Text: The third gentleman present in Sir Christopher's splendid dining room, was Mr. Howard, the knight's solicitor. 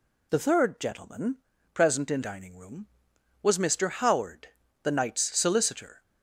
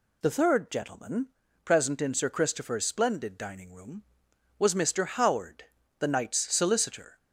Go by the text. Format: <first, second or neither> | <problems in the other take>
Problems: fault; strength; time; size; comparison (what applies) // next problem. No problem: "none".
second | pauses between "gentleman" and "present"; at 1.3 s; 0.38 s long; also in the second // skips "Sir Christopher's splendid"; at 2.2 s